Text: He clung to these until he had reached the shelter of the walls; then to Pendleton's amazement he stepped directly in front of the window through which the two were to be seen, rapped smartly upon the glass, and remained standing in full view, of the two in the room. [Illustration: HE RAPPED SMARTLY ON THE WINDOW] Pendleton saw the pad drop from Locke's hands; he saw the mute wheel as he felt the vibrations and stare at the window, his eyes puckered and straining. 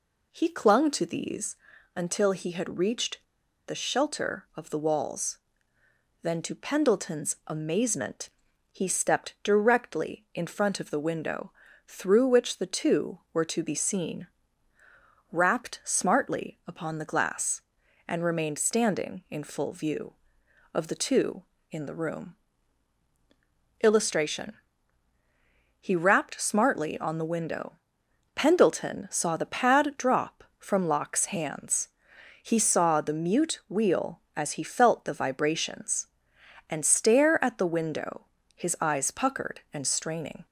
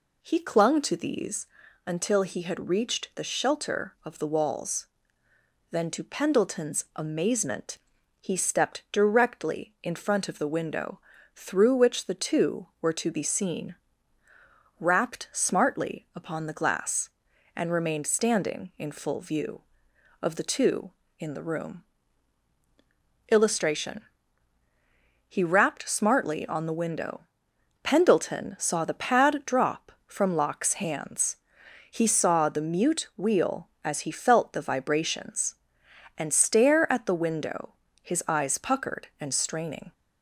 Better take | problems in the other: second | pauses between "these" and "until"; at 1.5 s; 0.38 s long; also in the second // pauses between "reached" and "the"; at 3.2 s; 0.44 s long // pauses between "amazement" and "he"; at 8.2 s; 0.42 s long; also in the second // pauses between "window" and "through"; slight; at 11.5 s; 0.36 s long; slight in the second // pauses between "WINDOW" and "Pendleton"; noticeable; at 27.7 s; 0.60 s long; noticeable in the second

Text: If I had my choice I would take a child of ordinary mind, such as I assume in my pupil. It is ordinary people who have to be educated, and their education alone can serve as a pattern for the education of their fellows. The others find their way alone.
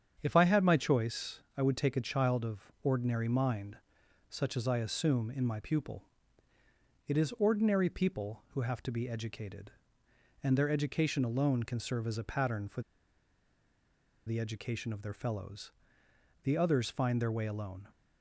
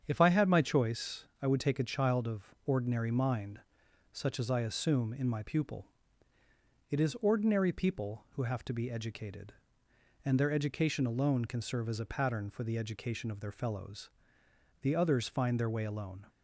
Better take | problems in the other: second | starts louder than the rest; strong; until 1.2 s; 8 dB; strong in the second // pauses between "for" and "the"; strong; at 12.8 s; 1.4 s long

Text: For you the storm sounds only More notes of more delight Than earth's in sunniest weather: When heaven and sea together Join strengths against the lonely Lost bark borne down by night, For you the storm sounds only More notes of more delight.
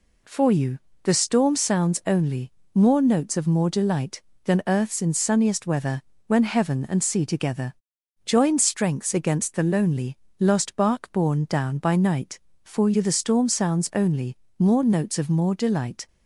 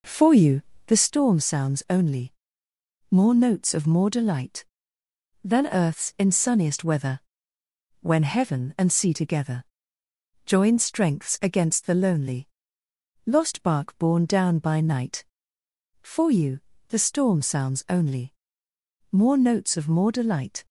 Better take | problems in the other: first | starts louder than the rest; noticeable; until 1.1 s; 5 dB // pauses between "you" and "the"; slight; at 0.6 s; 0.24 s long; slight in the first // pauses between "only" and "More"; noticeable; at 2.3 s; 0.78 s long; slight in the first // pauses between "together" and "Join"; noticeable; at 9.6 s; 0.82 s long; noticeable in the first // pauses between "lonely" and "Lost"; noticeable; at 12.4 s; 0.78 s long; slight in the first // pauses between "you" and "the"; slight; at 16.5 s; 0.30 s long // pauses between "only" and "More"; noticeable; at 18.3 s; 0.80 s long; slight in the first

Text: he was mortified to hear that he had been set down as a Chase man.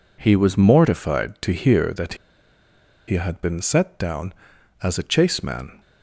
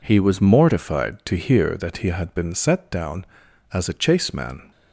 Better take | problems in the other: second | pauses between "that" and "he"; noticeable; at 2.1 s; 0.92 s long

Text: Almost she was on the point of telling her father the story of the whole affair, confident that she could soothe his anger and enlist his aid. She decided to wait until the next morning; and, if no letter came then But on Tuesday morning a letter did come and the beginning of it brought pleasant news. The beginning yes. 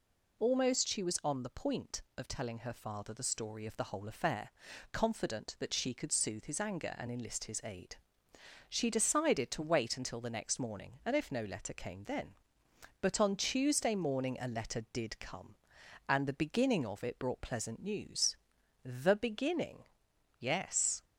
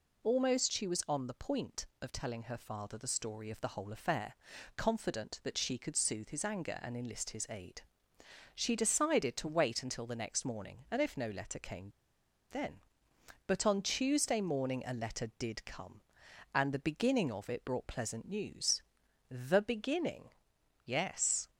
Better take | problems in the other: first | pauses between "came" and "then"; noticeable; at 11.8 s; 0.62 s long // pauses between "beginning" and "yes"; noticeable; at 20.2 s; 0.56 s long; noticeable in the first

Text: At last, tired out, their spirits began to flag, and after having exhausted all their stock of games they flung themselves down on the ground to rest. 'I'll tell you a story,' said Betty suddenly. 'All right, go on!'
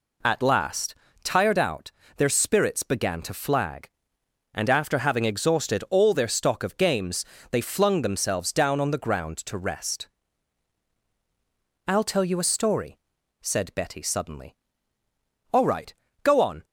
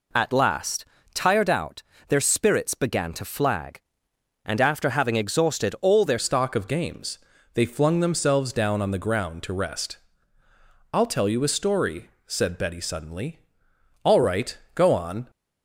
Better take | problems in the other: first | changes voice at "stock"; from 6.1 s on; 9.1 s long // pauses between "games" and "they"; slight; at 7.1 s; 0.36 s long; slight in the first

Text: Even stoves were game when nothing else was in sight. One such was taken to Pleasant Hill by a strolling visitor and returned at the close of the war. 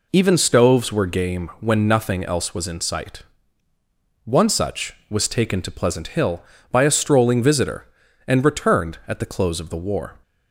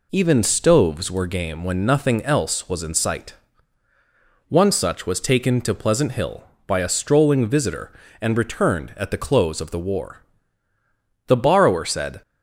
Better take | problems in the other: first | goes on to say "The borrower said"; noticeable; from 11.2 s on; 0.94 s long

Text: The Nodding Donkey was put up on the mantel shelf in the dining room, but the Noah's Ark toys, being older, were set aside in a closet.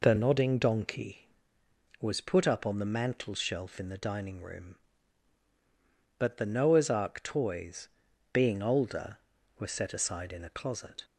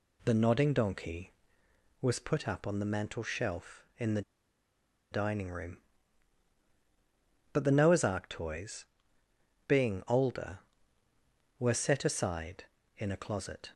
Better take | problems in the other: first | pauses between "the" and "dining"; noticeable; at 4.2 s; 0.90 s long

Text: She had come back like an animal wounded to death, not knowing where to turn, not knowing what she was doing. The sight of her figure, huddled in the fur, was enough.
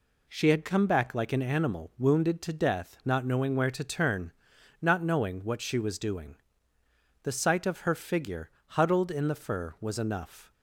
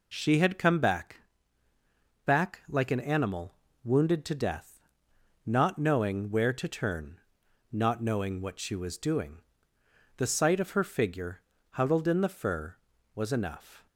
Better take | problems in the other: first | says "back" twice; at 2.2 s // pauses between "animal" and "wounded"; slight; at 3.5 s; 0.28 s long

